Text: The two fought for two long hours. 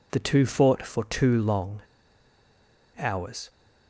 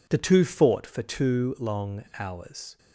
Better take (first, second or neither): second